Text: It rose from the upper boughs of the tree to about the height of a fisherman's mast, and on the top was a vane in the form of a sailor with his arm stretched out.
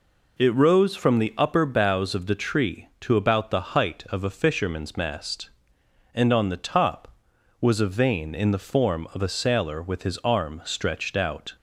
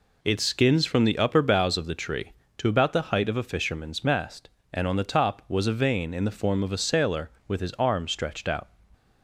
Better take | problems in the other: first | says "skins" for "rose"; at 0.3 s

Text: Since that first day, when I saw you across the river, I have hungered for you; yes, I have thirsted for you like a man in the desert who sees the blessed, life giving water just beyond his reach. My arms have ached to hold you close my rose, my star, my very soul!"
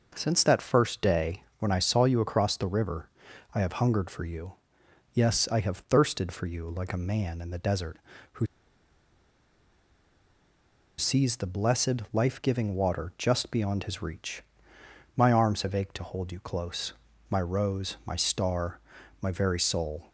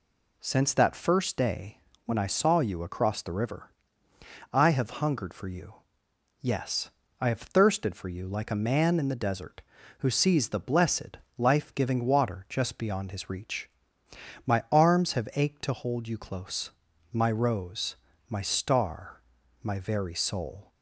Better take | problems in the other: second | pauses between "who" and "sees"; strong; at 8.4 s; 2.5 s long // pauses between "close" and "my"; slight; at 16.9 s; 0.36 s long; also in the second

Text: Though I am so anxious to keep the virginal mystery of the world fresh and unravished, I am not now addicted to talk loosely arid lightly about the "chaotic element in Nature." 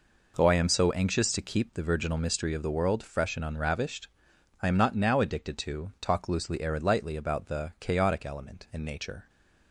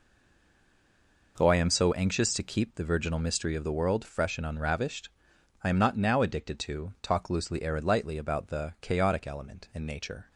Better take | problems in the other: first | stays silent before the first word; noticeable; until 1.3 s; 1.3 s long

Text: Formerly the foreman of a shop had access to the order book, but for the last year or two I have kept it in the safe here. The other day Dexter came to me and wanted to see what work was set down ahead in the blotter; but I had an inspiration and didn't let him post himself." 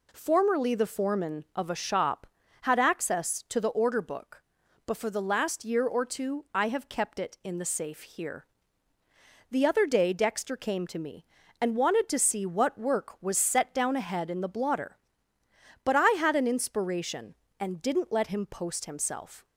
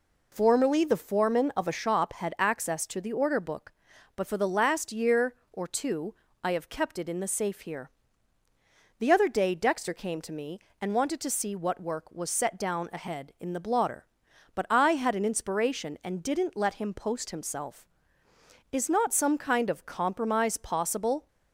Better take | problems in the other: first | pauses between "two" and "I"; slight; at 6.1 s; 0.28 s long // goes on to say "Is not some kind of compromise possible"; strong; from 18.7 s on; 2.5 s long

